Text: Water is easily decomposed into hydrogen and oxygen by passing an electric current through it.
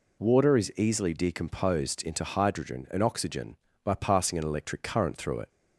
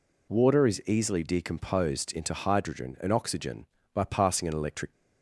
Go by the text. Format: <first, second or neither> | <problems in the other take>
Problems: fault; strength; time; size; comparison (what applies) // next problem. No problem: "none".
first | stops before "current through it"; at 4.9 s